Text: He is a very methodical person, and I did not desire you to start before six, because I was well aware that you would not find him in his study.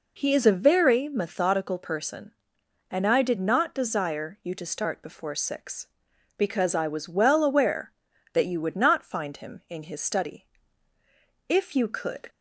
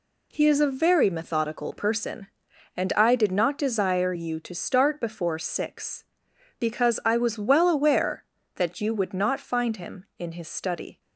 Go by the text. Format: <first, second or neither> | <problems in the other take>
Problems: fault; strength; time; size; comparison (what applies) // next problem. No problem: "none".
second | goes on to say "If you could"; noticeable; from 11.4 s on; 0.80 s long